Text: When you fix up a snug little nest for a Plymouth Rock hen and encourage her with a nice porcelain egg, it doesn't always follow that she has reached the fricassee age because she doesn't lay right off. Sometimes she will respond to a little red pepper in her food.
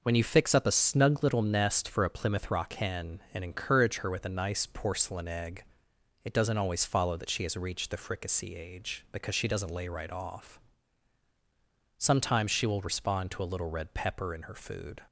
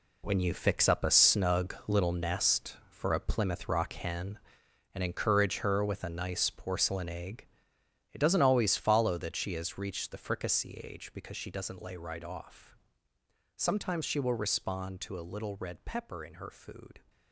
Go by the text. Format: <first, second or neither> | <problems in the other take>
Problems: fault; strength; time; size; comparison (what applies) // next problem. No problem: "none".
first | gets quieter; strong; throughout; 10.5 dB